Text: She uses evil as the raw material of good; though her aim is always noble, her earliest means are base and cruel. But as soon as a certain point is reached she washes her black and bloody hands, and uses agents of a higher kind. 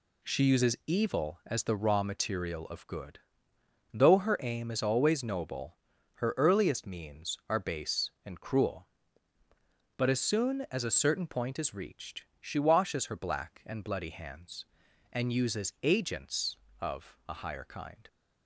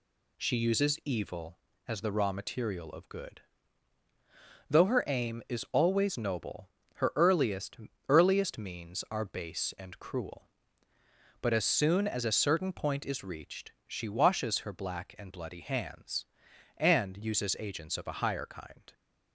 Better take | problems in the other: first | says "earliest" twice; at 8.0 s // pauses between "reached" and "she"; slight; at 13.7 s; 0.16 s long; slight in the first

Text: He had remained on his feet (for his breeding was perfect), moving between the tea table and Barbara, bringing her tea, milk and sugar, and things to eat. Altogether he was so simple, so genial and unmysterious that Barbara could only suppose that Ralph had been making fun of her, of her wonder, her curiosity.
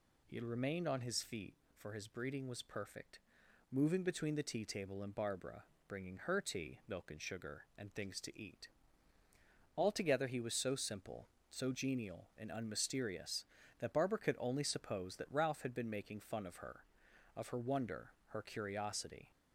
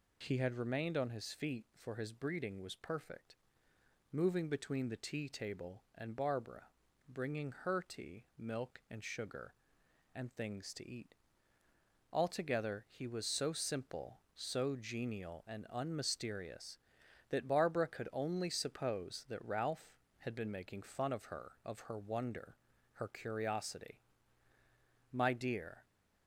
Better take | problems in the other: first | goes on to say "My dear"; noticeable; from 25.1 s on; 0.72 s long

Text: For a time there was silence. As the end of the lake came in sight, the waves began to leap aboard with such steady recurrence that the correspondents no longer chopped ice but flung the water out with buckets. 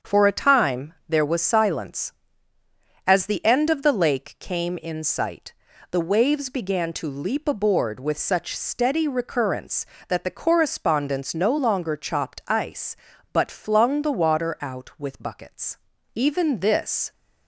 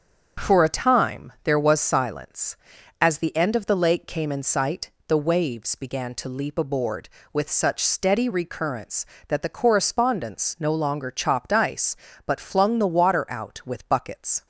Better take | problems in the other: second | starts louder than the rest; until 1.1 s; 7 dB; also in the second // goes on to say "Even this"; noticeable; from 16.1 s on; 0.96 s long

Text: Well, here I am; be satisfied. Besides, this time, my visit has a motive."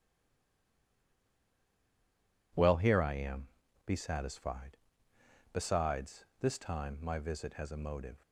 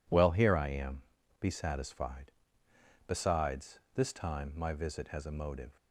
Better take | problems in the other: second | stays silent before the first word; until 2.5 s; 2.5 s long

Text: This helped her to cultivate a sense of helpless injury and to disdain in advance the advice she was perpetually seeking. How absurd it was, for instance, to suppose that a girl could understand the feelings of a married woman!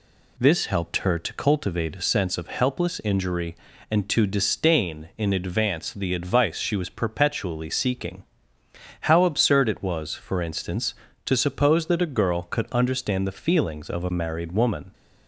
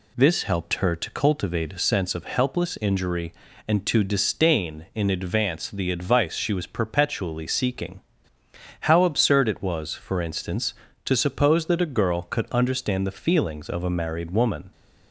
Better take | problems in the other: neither | none

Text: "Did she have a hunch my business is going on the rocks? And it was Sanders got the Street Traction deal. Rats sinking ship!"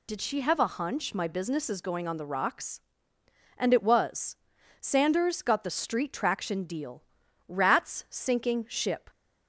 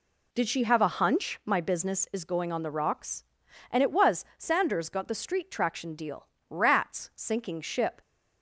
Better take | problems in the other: second | loses the start of "Did"; at 0.0 s; 75 ms // pauses between "was" and "Sanders"; noticeable; at 4.3 s; 0.46 s long

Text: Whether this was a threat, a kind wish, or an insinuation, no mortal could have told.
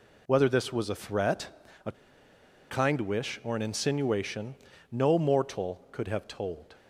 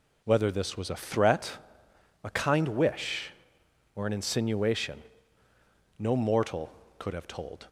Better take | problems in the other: second | pauses between "a" and "kind"; noticeable; at 1.9 s; 0.77 s long

